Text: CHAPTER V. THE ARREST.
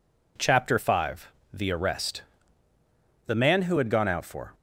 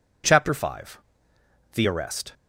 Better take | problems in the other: second | goes on to say "The man who had gone out for"; noticeable; from 3.2 s on; 1.2 s long

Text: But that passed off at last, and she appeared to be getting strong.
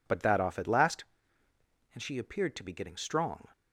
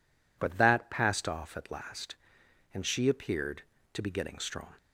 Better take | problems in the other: second | skips "passed"; at 0.3 s

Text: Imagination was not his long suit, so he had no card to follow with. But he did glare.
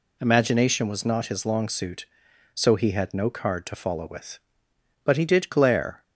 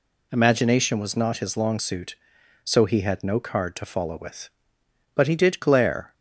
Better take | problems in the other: neither | none

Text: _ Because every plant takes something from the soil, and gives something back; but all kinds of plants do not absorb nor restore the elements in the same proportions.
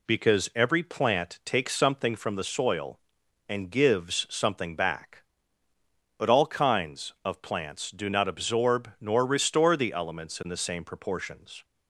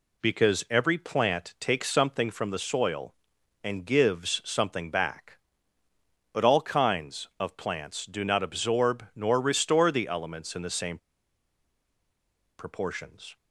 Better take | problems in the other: first | pauses between "same" and "proportions"; strong; at 10.9 s; 1.6 s long

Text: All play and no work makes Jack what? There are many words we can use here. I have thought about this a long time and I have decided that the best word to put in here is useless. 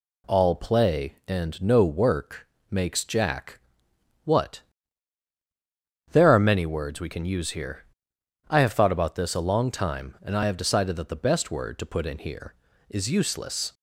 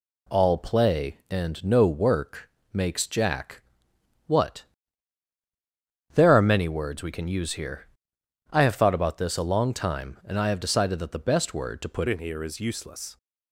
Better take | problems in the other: first | pauses between "work" and "makes"; slight; at 2.4 s; 0.24 s long; slight in the first // pauses between "Jack" and "what"; noticeable; at 3.6 s; 0.66 s long; noticeable in the first // changes voice at "in"; from 12.0 s on; 1.1 s long

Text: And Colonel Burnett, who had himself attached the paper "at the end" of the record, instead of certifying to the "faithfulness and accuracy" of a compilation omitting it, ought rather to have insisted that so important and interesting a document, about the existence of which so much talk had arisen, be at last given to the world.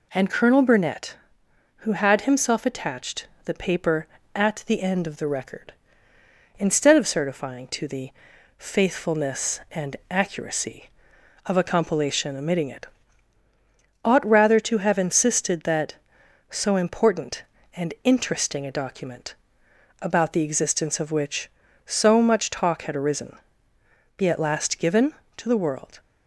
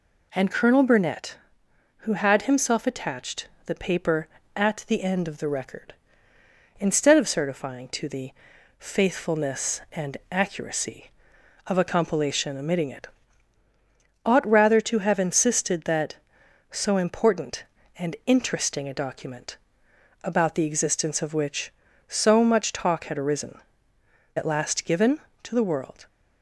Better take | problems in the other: first | pauses between "attached" and "the"; slight; at 3.4 s; 0.18 s long; slight in the first // pauses between "the" and "faithfulness"; noticeable; at 8.3 s; 0.46 s long; noticeable in the first // skips "be"; at 23.9 s

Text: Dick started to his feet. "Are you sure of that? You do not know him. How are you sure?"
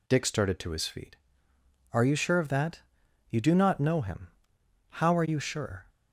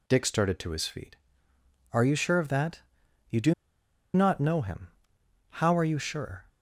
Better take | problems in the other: first | pauses between "do" and "not"; noticeable; at 3.5 s; 0.62 s long

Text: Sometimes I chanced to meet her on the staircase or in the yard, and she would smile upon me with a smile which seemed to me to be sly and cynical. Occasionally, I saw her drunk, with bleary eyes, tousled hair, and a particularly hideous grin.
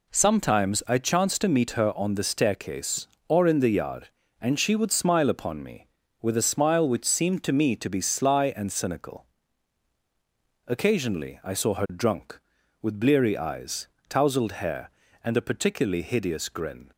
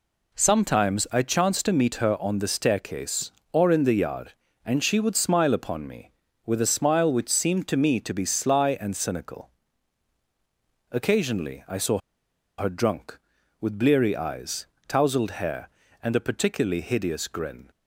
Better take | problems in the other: first | pauses between "saw" and "her"; noticeable; at 11.9 s; 0.60 s long

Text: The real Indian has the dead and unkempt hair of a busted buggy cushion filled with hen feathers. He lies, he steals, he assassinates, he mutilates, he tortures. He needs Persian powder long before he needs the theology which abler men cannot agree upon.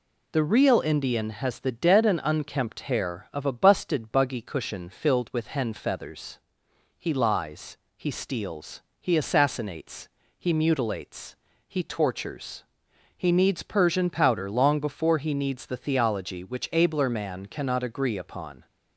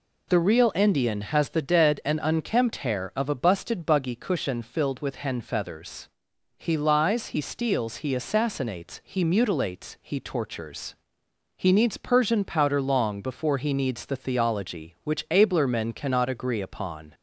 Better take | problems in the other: second | says "man" for "men"; at 17.0 s

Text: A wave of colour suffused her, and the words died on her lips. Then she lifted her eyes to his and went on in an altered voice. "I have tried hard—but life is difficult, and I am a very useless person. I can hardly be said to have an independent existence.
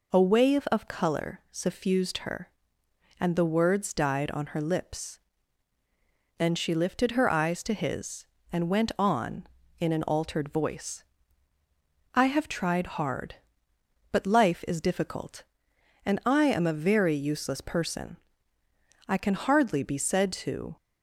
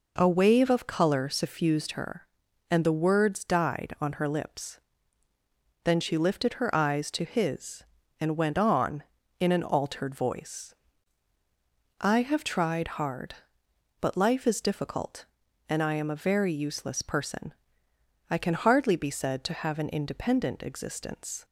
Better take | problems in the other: second | stops before "have an independent existence"; at 20.7 s

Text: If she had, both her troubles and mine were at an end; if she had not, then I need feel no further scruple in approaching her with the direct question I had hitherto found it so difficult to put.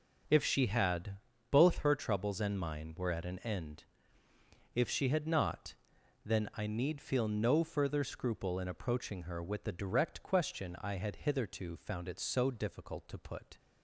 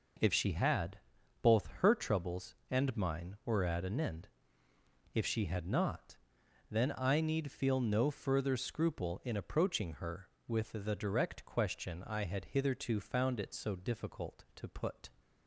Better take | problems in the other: neither | none

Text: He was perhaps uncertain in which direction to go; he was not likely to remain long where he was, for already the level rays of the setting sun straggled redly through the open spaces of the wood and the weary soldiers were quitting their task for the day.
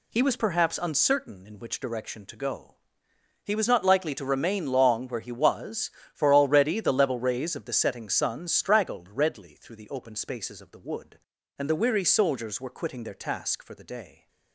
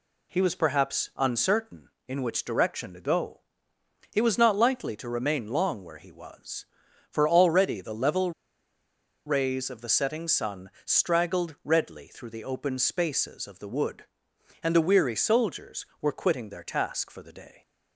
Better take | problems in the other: first | pauses between "level" and "rays"; noticeable; at 8.3 s; 0.95 s long

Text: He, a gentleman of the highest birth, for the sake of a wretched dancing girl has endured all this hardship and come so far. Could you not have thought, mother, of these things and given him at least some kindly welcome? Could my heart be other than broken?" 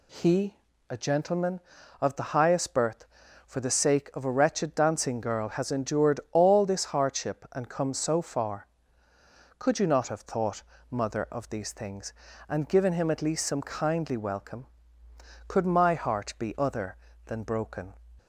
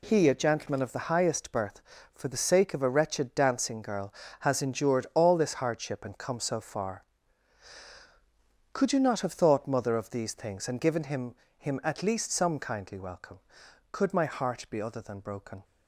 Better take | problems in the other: first | says "him" twice; at 11.5 s

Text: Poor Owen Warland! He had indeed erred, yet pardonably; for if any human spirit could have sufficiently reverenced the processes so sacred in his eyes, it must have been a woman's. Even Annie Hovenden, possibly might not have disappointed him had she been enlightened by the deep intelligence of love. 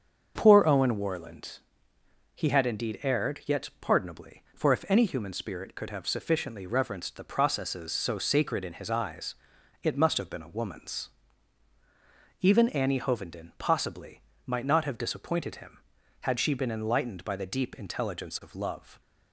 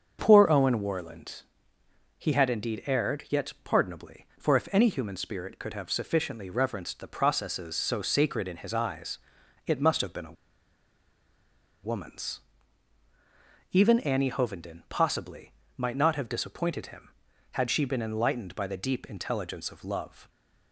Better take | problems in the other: first | starts louder than the rest; until 1.2 s; 7 dB; also in the first // pauses between "a" and "woman's"; strong; at 10.3 s; 1.4 s long // pauses between "possibly" and "might"; slight; at 15.5 s; 0.24 s long; slight in the first

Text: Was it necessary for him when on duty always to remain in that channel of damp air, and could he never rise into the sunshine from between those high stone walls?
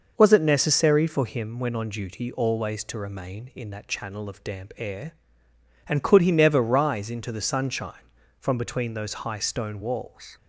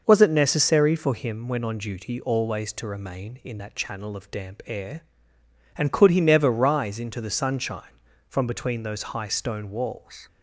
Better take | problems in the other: neither | none

